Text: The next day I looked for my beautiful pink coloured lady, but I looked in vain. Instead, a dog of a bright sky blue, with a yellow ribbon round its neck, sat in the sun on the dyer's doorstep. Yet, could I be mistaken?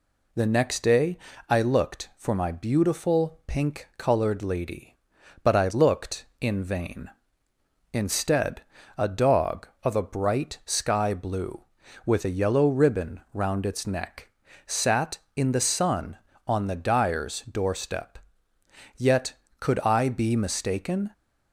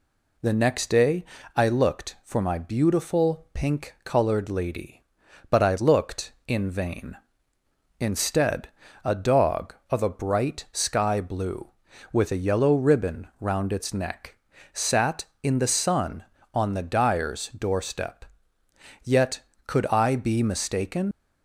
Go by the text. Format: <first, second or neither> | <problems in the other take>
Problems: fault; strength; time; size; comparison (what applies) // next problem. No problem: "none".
first | pauses between "day" and "I"; slight; at 1.2 s; 0.32 s long; slight in the first // leaves "mistaken" unfinished; at 21.1 s; 80 ms